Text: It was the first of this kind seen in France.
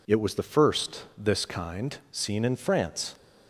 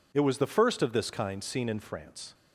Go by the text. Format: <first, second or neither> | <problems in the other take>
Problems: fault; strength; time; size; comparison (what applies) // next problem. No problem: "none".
second | skips "of"; at 1.0 s // pauses between "kind" and "seen"; slight; at 1.9 s; 0.16 s long